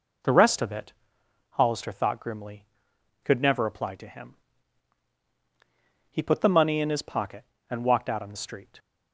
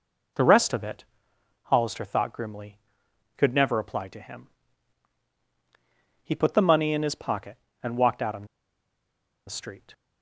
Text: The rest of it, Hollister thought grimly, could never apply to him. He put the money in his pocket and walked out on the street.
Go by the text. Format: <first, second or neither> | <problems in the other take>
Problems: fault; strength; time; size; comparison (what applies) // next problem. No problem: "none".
first | pauses between "on" and "the"; at 8.4 s; 1.0 s long